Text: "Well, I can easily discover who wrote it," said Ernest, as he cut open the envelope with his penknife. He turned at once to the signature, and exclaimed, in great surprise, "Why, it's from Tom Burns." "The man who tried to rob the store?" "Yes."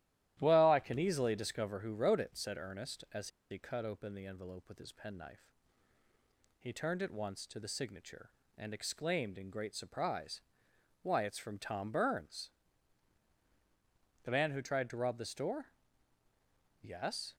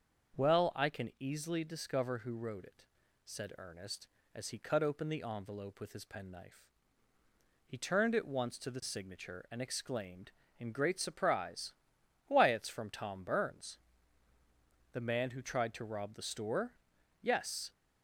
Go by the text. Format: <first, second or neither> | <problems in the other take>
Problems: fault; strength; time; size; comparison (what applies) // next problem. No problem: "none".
second | starts louder than the rest; strong; until 1.4 s; 13 dB; also in the second // pauses between "as" and "he"; slight; at 3.2 s; 0.22 s long